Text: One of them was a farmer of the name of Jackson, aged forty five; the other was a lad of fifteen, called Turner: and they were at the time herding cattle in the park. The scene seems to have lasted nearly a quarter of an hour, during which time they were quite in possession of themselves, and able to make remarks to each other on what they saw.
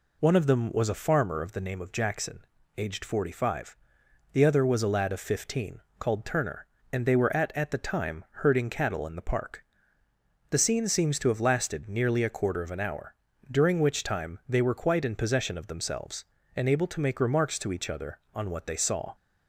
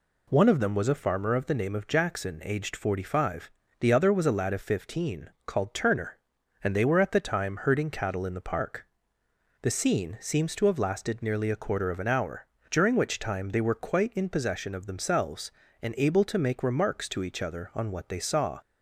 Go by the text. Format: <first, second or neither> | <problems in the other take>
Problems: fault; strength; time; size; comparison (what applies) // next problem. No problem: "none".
second | says "at" twice; at 7.5 s